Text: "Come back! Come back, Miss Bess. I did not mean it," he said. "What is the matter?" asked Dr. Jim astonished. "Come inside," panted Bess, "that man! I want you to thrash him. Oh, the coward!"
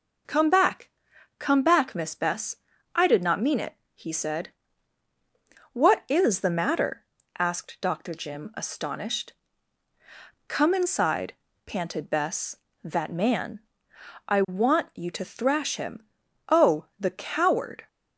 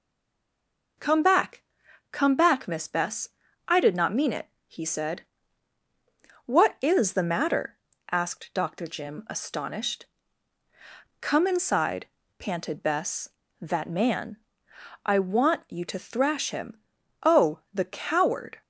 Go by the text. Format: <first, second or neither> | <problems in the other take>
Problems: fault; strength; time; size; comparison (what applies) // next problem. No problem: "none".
first | stays silent before the first word; until 0.9 s; 0.9 s long